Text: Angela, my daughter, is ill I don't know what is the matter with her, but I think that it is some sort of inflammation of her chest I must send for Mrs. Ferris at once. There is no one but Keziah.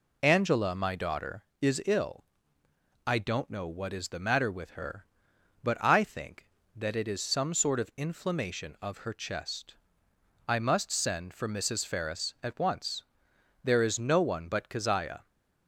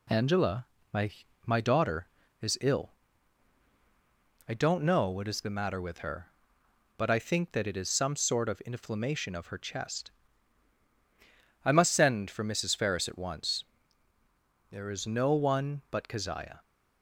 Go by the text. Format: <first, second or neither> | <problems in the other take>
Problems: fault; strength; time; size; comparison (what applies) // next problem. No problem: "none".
first | says "my" twice; at 1.4 s // pauses between "ill" and "I"; strong; at 2.9 s; 1.5 s long; noticeable in the first // pauses between "chest" and "I"; strong; at 10.1 s; 1.5 s long; noticeable in the first